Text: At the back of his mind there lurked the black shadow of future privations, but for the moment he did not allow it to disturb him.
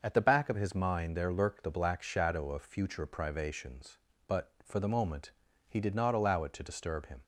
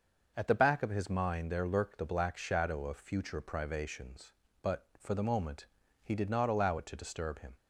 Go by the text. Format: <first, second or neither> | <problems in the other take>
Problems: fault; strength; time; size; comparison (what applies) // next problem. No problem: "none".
neither | starts louder than the rest; noticeable; the same in both // pauses between "moment" and "he"; the same in both